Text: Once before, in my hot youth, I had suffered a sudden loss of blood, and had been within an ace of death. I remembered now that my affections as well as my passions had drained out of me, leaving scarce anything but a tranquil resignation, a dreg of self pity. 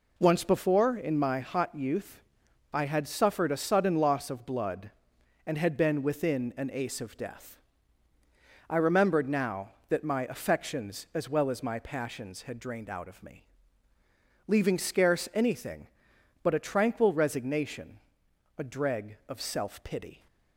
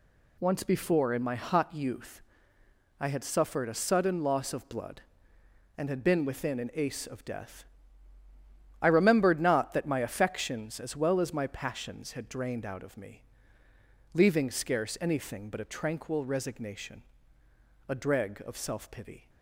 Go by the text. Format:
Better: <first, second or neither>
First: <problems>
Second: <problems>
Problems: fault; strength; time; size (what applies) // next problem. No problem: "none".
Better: first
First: none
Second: says "not" for "now"; at 9.4 s